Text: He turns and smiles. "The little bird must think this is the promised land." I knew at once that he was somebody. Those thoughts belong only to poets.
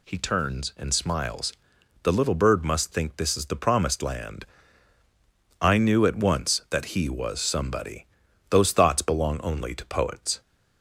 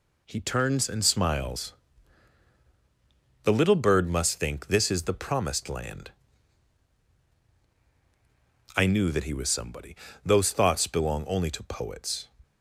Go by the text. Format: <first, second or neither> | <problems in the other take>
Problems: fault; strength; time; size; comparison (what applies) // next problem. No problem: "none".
first | skips "at once"; at 9.1 s